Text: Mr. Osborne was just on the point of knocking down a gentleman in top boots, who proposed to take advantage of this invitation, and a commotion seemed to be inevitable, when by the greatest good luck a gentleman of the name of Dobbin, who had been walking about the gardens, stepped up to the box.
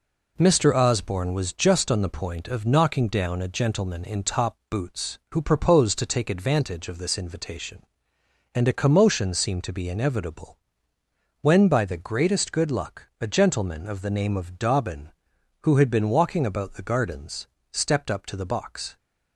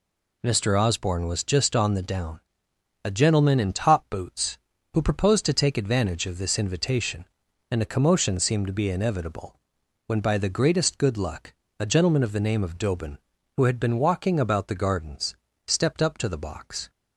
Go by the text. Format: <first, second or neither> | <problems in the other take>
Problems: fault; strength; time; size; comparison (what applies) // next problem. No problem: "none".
first | skips "point of knocking"; at 2.0 s // pauses between "down" and "a"; noticeable; at 2.3 s; 0.64 s long // pauses between "luck" and "a"; slight; at 11.5 s; 0.24 s long